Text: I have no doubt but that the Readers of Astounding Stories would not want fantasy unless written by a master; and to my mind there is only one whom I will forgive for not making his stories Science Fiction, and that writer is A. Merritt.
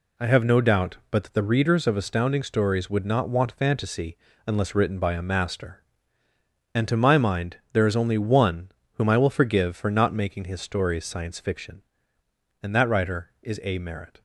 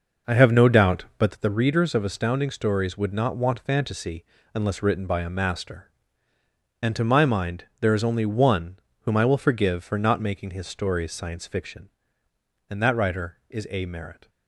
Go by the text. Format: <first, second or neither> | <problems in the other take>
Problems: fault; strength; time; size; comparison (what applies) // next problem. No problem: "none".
first | starts louder than the rest; noticeable; until 1.5 s; 5.5 dB // pauses between "fantasy" and "unless"; slight; at 4.2 s; 0.30 s long; slight in the first // pauses between "mind" and "there"; slight; at 7.6 s; 0.16 s long; slight in the first // pauses between "one" and "whom"; slight; at 8.7 s; 0.22 s long; slight in the first